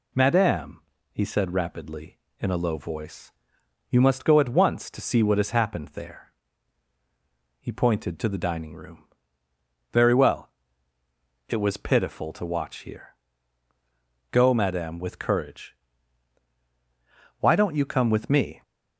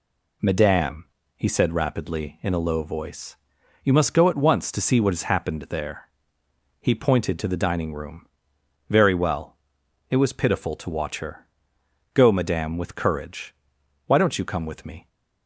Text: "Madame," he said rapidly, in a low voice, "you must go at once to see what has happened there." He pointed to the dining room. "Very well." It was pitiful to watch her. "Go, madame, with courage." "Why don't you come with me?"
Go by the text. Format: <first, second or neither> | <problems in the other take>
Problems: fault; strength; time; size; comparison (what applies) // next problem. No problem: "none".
second | says "here" for "her"; at 12.7 s